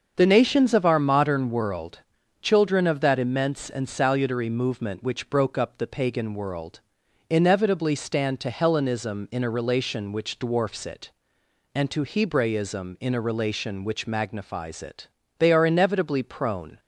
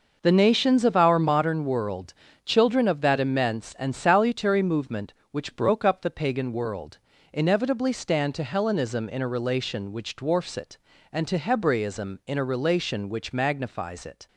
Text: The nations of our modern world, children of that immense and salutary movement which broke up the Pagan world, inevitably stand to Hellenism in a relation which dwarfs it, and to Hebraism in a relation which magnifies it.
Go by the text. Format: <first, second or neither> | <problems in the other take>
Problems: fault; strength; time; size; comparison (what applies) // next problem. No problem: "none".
second | starts louder than the rest; until 1.1 s; 6.5 dB // goes on to say "They are inevitably prone"; from 15.3 s on; 1.4 s long